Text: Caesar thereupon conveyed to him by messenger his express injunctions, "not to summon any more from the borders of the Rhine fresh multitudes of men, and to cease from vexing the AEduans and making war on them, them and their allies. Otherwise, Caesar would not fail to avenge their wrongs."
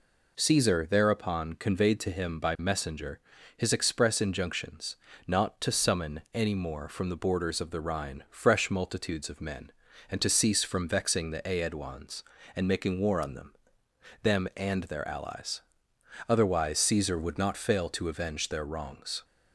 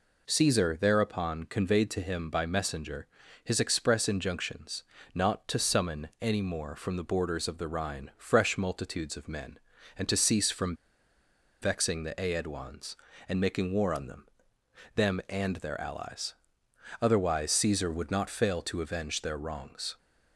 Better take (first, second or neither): first